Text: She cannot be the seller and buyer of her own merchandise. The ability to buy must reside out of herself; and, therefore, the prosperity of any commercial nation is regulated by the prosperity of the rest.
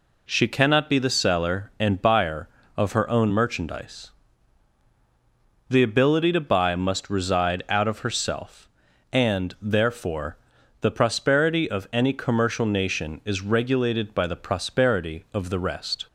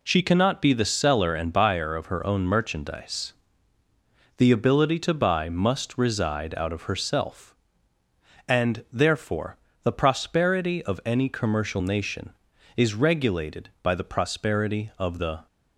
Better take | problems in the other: first | stops before "rest"; at 15.4 s

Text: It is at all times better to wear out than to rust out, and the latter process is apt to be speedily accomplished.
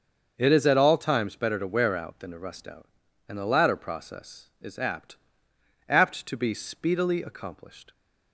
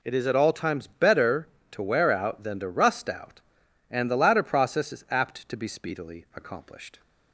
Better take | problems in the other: second | starts louder than the rest; until 1.3 s; 6.5 dB // says "apt" twice; at 5.8 s

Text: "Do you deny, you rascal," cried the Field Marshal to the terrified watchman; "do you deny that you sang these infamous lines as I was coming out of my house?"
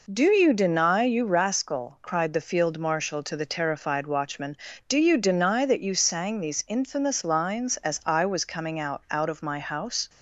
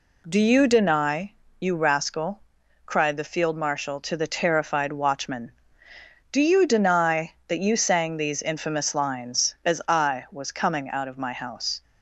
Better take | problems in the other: second | says "out" twice; at 9.0 s

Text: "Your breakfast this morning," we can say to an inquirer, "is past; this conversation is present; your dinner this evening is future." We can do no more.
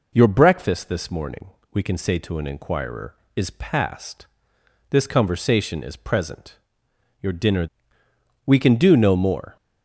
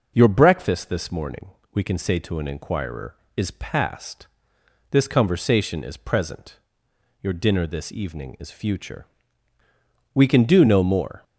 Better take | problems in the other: second | skips "this evening is future"; at 8.0 s

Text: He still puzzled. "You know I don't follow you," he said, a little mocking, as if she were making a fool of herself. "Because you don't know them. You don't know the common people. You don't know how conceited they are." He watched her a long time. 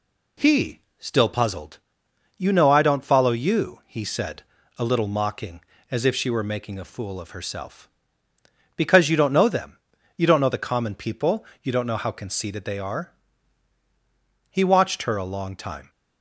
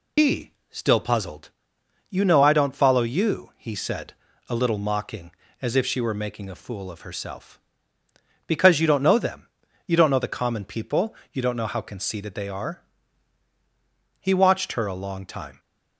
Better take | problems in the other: first | loses the start of "He"; at 0.1 s; 75 ms // pauses between "He" and "still"; slight; at 0.5 s; 0.18 s long; slight in the first

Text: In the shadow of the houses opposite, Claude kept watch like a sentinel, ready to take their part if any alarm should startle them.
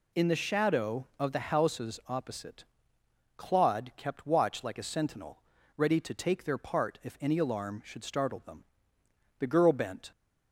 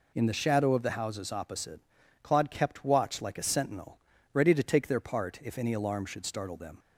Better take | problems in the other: second | goes on to say "The girl bent"; noticeable; from 9.3 s on; 0.72 s long

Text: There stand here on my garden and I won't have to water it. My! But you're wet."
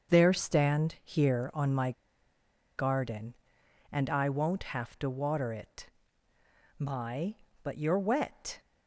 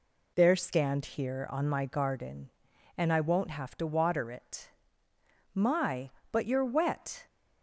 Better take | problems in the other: second | starts louder than the rest; until 1.1 s; 6.5 dB // pauses between "my" and "garden"; noticeable; at 1.9 s; 0.85 s long

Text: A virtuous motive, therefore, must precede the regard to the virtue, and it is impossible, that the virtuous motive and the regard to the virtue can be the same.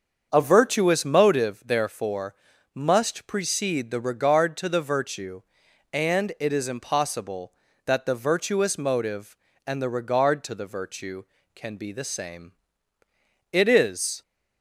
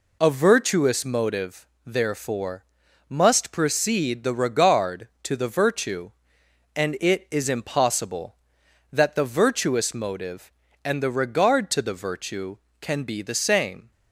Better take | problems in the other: second | starts louder than the rest; until 1.3 s; 7 dB // goes on to say "It is"; noticeable; from 13.5 s on; 0.70 s long

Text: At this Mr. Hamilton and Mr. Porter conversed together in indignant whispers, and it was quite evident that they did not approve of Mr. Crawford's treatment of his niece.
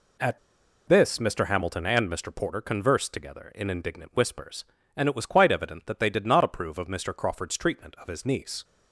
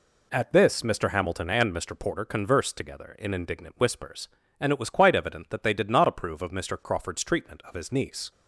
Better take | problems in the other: second | pauses between "At" and "this"; noticeable; at 0.3 s; 0.50 s long

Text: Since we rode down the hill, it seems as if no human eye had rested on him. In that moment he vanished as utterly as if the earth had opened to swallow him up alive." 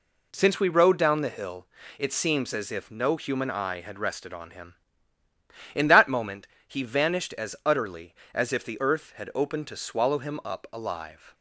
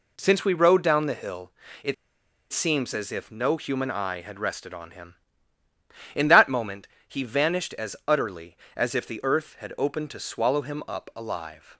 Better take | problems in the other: first | pauses between "it" and "seems"; noticeable; at 1.9 s; 0.58 s long // pauses between "moment" and "he"; slight; at 6.8 s; 0.18 s long; slight in the first

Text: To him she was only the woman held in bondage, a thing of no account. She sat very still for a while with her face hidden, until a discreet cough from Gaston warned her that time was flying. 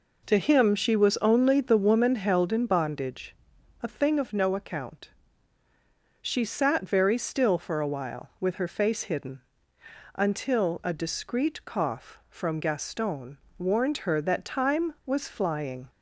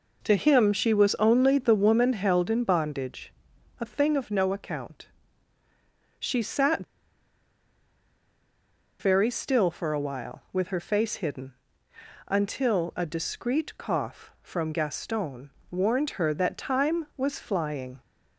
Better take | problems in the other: first | pauses between "sat" and "very"; strong; at 6.8 s; 2.1 s long // pauses between "Gaston" and "warned"; slight; at 15.4 s; 0.22 s long; slight in the first

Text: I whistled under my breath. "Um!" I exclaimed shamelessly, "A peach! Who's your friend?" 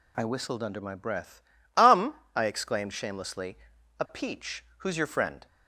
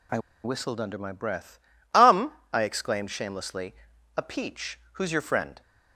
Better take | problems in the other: first | pauses between "I" and "whistled"; slight; at 0.1 s; 0.25 s long

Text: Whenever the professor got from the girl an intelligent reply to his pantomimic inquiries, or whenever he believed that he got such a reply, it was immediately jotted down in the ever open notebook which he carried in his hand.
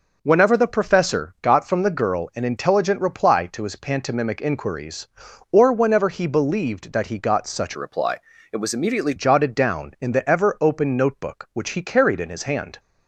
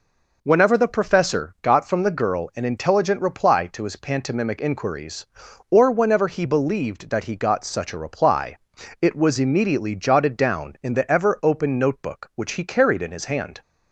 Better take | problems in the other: second | changes voice from "a" to "immediately"; from 7.7 to 9.1 s; 1.4 s long

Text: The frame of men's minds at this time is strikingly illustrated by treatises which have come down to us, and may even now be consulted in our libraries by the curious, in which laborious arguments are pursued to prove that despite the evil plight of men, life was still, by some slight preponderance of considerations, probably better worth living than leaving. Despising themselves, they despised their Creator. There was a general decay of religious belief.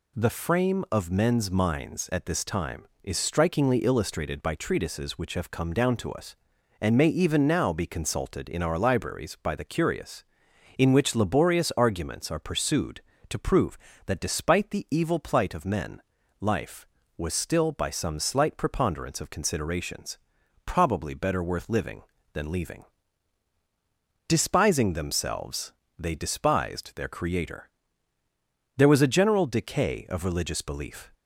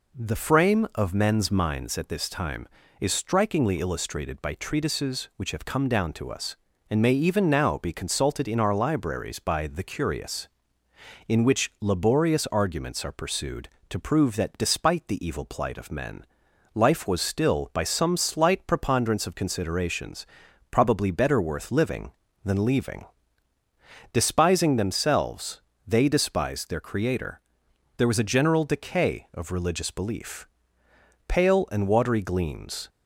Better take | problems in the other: first | goes on to say "Pale and watery gleams"; from 31.2 s on; 1.6 s long

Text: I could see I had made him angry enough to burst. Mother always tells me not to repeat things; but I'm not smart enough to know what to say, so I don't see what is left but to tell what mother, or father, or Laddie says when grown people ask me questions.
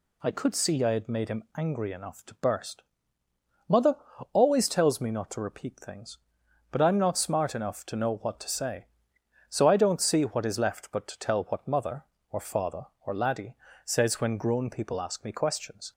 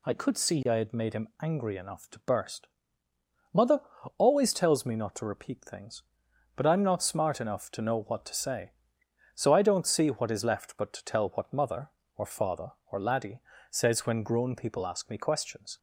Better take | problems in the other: neither | pauses between "Mother" and "always"; the same in both // pauses between "Laddie" and "says"; slight; the same in both

